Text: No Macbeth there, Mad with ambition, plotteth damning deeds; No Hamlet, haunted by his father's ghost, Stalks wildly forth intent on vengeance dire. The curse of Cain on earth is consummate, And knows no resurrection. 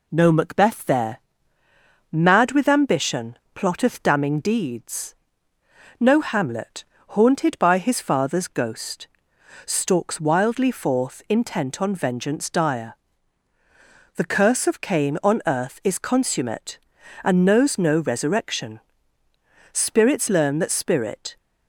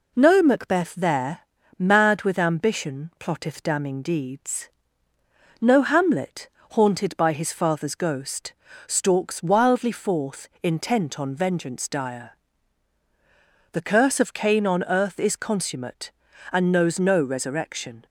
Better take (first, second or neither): second